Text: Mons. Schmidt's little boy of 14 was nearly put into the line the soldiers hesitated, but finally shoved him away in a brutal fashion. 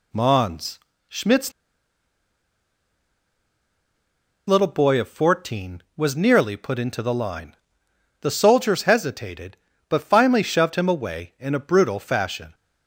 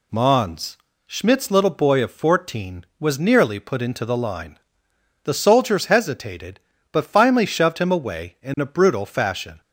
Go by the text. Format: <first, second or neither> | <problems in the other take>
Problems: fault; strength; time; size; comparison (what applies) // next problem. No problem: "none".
second | pauses between "Schmidt's" and "little"; strong; at 1.5 s; 2.9 s long // pauses between "line" and "the"; noticeable; at 7.5 s; 0.68 s long; noticeable in the second